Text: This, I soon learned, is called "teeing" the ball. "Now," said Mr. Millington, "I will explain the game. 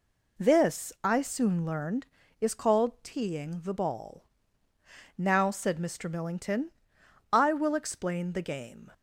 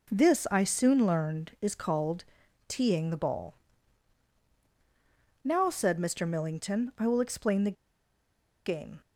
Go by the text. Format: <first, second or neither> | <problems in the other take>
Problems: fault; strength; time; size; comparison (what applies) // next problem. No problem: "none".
first | pauses between "called" and "teeing"; at 2.2 s; 0.42 s long // pauses between "the" and "game"; noticeable; at 7.7 s; 0.92 s long